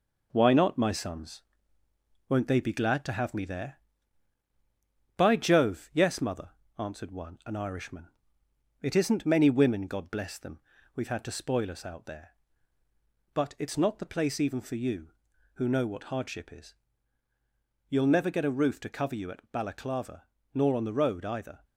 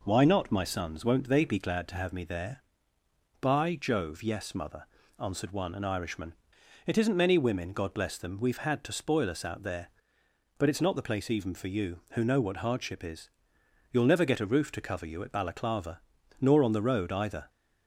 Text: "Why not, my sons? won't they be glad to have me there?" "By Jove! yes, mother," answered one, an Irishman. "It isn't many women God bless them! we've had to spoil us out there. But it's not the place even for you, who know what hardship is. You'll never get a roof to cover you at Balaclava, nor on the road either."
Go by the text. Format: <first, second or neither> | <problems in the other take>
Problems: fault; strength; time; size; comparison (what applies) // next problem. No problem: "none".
second | gets quieter; noticeable; throughout; 5 dB